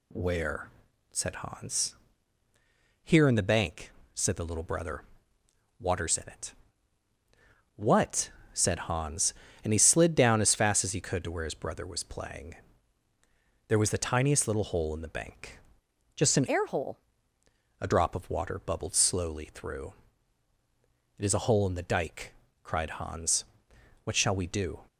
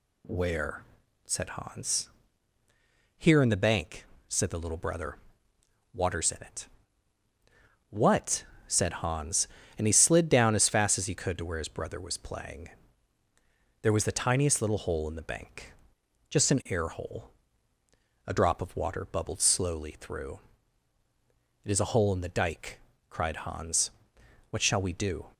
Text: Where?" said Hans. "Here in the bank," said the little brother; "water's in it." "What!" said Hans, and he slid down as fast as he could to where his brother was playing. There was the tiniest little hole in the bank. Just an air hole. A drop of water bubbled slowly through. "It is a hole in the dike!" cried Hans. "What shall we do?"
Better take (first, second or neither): second